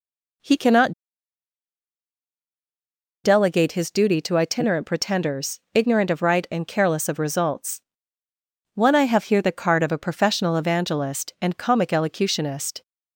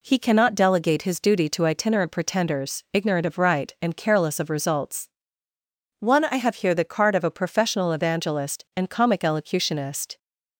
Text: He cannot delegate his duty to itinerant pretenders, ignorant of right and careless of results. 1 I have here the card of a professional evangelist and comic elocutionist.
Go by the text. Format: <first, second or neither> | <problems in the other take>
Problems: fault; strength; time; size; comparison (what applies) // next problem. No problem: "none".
second | pauses between "cannot" and "delegate"; strong; at 0.9 s; 2.3 s long